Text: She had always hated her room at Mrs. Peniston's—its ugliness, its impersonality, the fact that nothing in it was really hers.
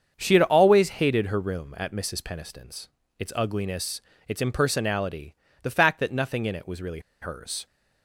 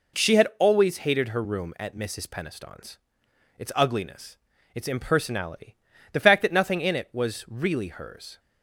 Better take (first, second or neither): second